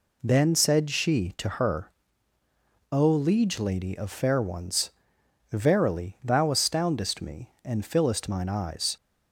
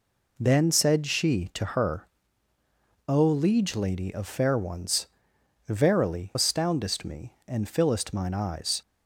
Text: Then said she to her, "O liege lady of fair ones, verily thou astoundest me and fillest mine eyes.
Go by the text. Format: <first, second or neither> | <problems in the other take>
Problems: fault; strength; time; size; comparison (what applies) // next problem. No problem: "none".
first | skips "thou"; at 6.3 s